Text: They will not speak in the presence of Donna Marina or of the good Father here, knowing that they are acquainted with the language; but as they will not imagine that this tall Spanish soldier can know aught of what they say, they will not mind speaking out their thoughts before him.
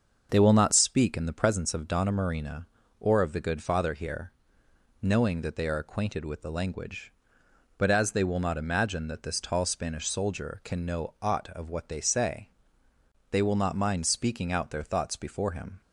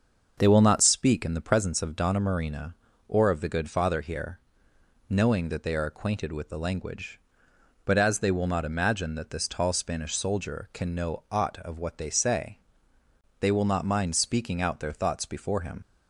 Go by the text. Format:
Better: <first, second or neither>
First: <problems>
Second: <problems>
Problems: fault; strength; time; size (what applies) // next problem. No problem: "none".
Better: first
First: starts louder than the rest; until 1.3 s; 6.5 dB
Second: starts louder than the rest; until 1.3 s; 6.5 dB // leaves "him" unfinished; at 15.8 s; 75 ms